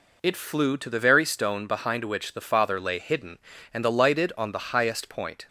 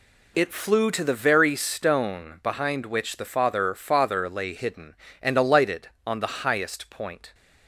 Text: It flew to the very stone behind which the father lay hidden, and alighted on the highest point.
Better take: first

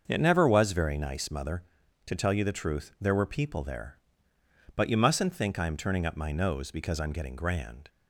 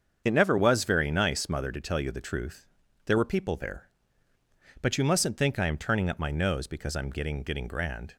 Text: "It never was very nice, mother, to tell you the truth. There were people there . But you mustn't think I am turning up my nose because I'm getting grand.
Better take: first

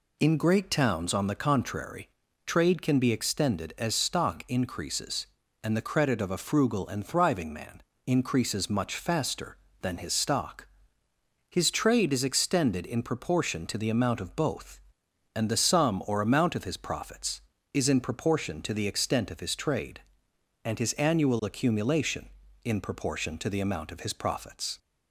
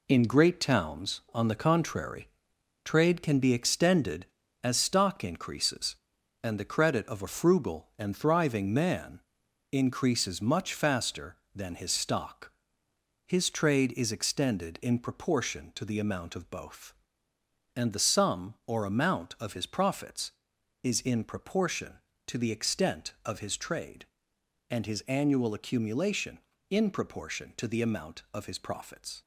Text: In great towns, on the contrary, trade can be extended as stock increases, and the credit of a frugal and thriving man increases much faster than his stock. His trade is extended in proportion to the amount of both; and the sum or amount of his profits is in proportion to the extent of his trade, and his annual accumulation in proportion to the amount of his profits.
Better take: first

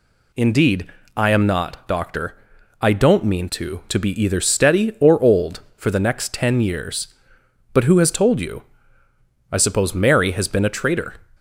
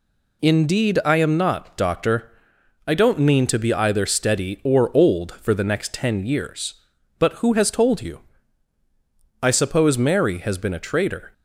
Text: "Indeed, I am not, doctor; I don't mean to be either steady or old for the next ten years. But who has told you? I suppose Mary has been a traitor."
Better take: second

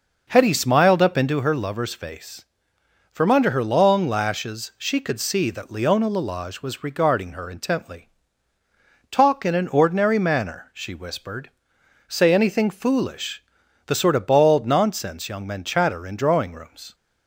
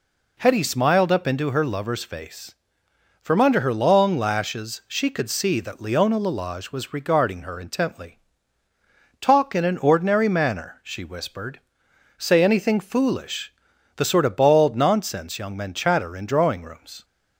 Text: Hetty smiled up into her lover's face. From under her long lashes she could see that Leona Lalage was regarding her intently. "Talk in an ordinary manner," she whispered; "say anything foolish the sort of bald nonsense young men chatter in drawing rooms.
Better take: second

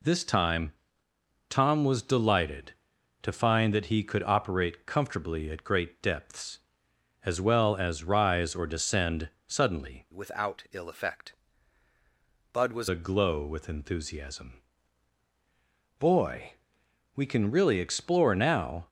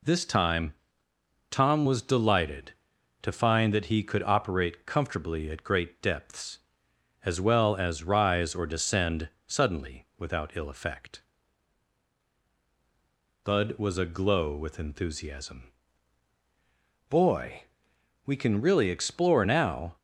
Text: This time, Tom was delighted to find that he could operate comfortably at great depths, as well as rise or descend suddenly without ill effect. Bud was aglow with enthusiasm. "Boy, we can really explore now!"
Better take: second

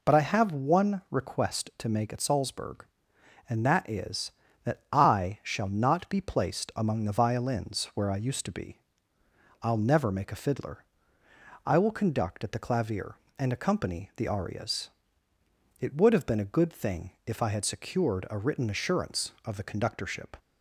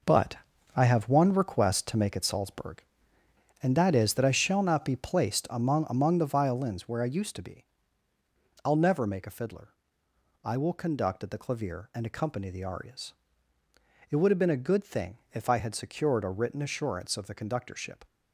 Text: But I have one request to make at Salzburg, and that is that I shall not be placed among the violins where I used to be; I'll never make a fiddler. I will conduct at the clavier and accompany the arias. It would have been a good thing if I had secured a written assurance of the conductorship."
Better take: first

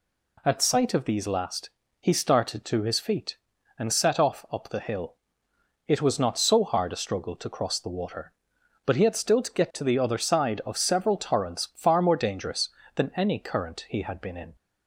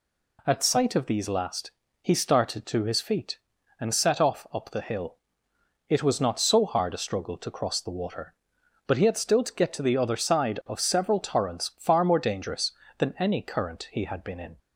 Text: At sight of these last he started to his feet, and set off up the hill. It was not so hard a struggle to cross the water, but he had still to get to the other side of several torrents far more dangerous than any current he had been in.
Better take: neither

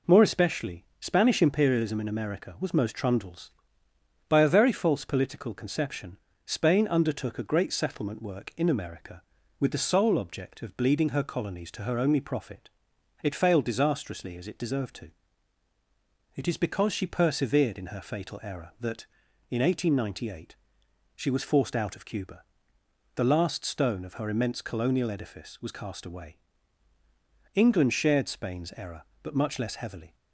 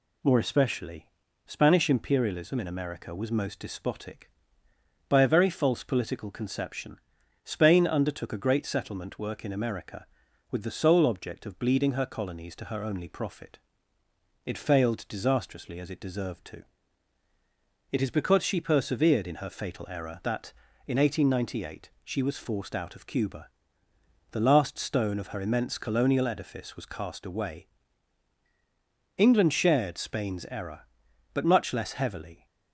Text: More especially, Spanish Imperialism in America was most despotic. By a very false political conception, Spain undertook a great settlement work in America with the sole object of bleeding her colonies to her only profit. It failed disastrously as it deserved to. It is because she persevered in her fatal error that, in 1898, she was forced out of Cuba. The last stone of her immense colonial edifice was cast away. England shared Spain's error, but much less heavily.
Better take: second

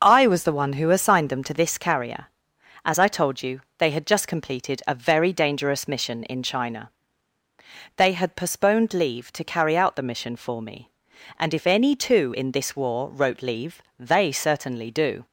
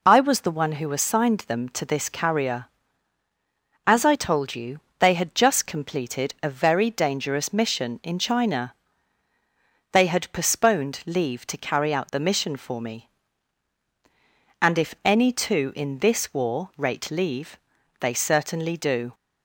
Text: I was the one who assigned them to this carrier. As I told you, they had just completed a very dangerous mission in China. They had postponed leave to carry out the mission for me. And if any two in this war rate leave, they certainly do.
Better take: second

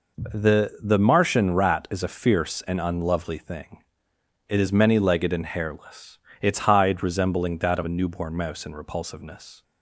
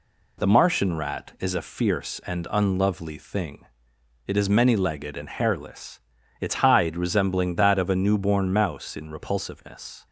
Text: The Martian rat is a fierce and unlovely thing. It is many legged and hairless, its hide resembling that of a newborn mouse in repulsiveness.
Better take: second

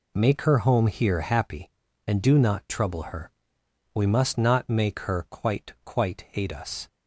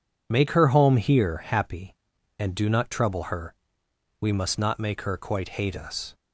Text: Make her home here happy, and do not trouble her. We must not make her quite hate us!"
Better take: second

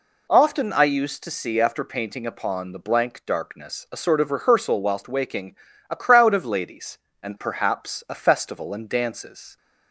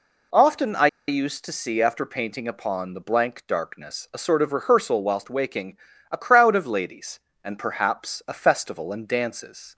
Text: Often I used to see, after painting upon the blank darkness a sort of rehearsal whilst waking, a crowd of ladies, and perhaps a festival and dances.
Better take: first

